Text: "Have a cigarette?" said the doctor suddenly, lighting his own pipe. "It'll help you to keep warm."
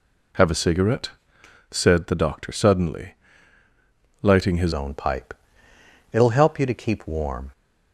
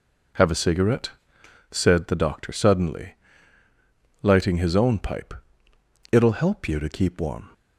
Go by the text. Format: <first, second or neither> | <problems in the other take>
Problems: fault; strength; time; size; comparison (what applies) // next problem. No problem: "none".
second | changes voice at "own"; from 4.7 s on; 2.8 s long